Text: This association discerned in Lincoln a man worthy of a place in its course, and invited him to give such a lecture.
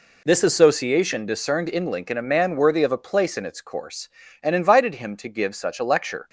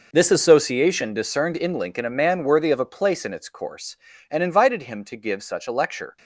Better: first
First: none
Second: gets quieter; strong; throughout; 13.5 dB

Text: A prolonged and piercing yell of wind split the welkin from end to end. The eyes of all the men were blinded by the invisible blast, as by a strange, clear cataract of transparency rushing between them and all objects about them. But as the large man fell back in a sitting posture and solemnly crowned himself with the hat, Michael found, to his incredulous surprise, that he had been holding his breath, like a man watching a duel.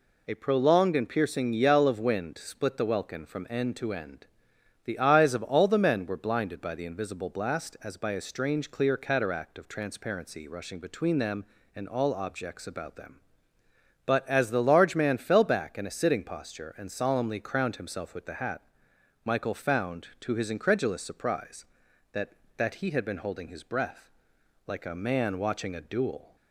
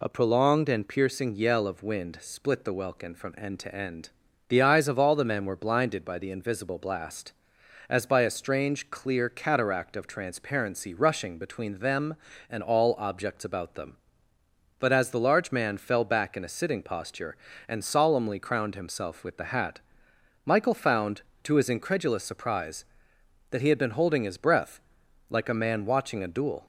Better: second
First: says "that" twice; at 22.5 s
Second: none

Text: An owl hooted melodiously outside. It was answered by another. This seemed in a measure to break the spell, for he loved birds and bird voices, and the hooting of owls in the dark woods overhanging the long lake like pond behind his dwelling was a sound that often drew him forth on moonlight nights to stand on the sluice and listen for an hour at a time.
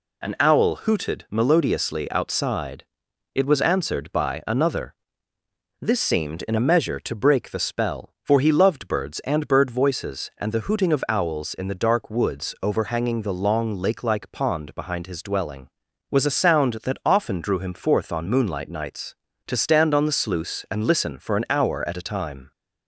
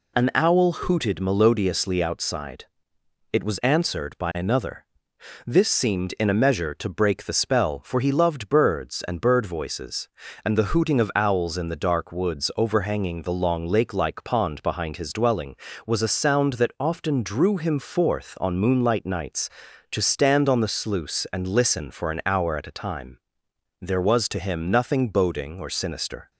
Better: first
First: none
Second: goes on to say "There was to him nothing boding or sinister"; strong; from 23.8 s on; 2.4 s long

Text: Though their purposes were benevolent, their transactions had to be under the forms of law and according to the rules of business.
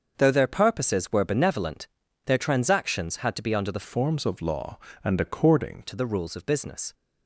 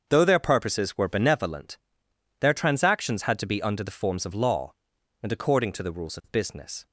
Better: second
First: starts louder than the rest; until 1.1 s; 6.5 dB // changes voice from "forms" to "according"; from 3.8 to 5.8 s; 2.0 s long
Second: starts louder than the rest; until 1.1 s; 7 dB

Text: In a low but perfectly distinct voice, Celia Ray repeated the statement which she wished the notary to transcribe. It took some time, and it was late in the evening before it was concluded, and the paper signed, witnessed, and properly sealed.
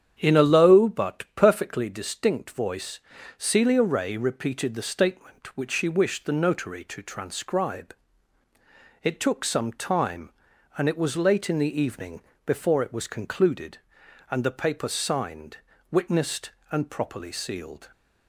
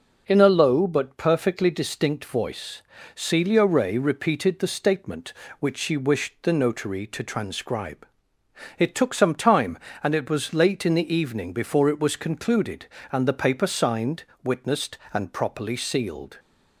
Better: second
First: starts louder than the rest; strong; until 1.9 s; 9 dB // pauses between "evening" and "before"; slight; at 12.2 s; 0.24 s long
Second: none

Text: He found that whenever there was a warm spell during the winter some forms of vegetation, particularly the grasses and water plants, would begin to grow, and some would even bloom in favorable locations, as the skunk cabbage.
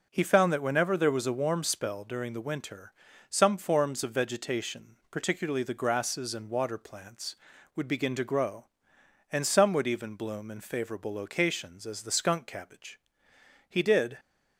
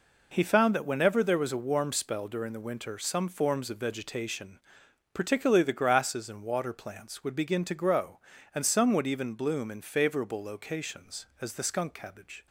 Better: second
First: pauses between "winter" and "some"; at 2.9 s; 0.38 s long // goes on to say "He did"; from 13.6 s on; 0.50 s long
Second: none

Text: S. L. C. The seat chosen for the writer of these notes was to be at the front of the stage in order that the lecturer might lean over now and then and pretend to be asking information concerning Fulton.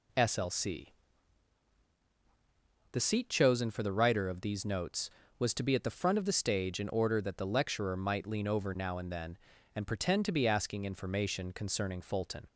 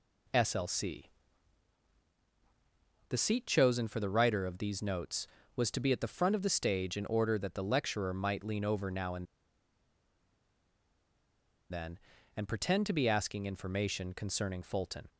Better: first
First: pauses between "C" and "The"; strong; at 0.8 s; 2.0 s long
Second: pauses between "C" and "The"; strong; at 1.0 s; 2.0 s long // pauses between "and" and "then"; strong; at 9.2 s; 2.4 s long

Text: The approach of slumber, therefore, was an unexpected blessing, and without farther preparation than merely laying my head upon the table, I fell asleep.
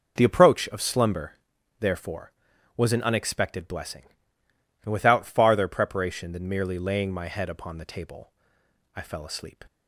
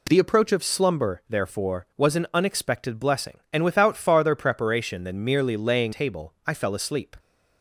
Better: first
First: none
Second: skips "my head upon the"; at 5.9 s

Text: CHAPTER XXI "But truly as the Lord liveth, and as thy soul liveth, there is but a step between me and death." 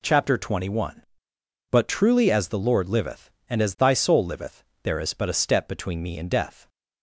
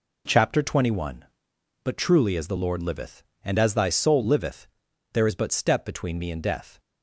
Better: first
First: none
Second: skips "a"; at 5.5 s

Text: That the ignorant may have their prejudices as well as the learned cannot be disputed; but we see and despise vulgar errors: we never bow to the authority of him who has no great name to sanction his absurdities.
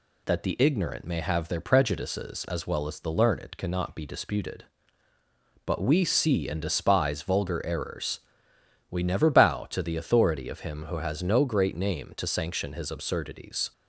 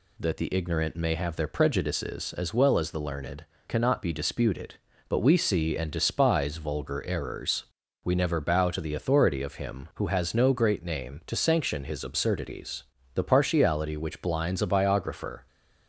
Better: first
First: none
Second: pauses between "learned" and "cannot"; slight; at 3.4 s; 0.22 s long // goes on to say "The partiality which blinds a biographer"; strong; from 13.1 s on; 2.3 s long

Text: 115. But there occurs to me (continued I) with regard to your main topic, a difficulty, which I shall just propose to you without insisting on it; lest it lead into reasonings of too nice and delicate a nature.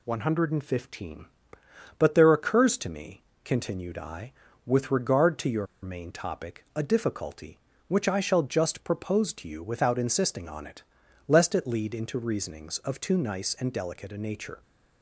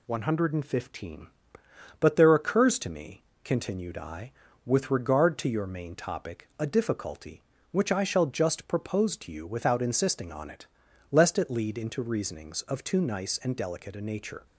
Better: second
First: pauses between "your" and "main"; slight; at 5.6 s; 0.17 s long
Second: none

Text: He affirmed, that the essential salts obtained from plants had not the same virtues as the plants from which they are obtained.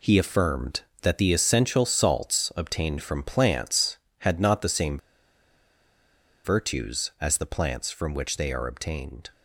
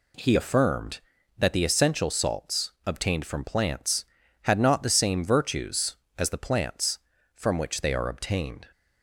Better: second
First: pauses between "same" and "virtues"; strong; at 4.9 s; 1.4 s long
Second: none

